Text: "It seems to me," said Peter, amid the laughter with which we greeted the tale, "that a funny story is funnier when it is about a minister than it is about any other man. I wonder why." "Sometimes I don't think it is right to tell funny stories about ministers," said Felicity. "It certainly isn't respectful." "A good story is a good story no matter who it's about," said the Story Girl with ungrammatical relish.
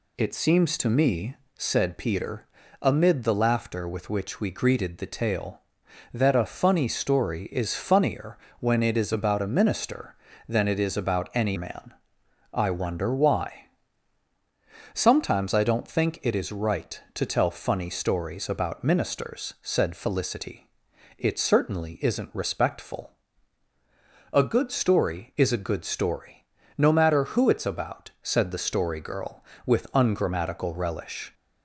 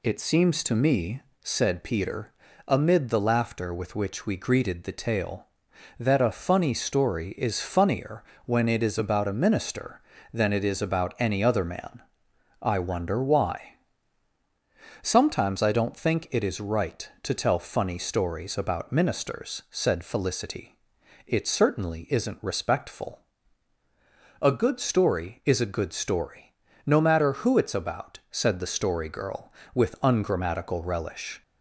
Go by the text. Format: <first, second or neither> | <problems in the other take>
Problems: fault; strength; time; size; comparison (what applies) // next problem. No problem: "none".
second | pauses between "funnier" and "when"; slight; at 8.3 s; 0.24 s long; slight in the second // skips "other"; at 11.5 s // pauses between "story" and "no"; at 26.3 s; 0.40 s long; also in the second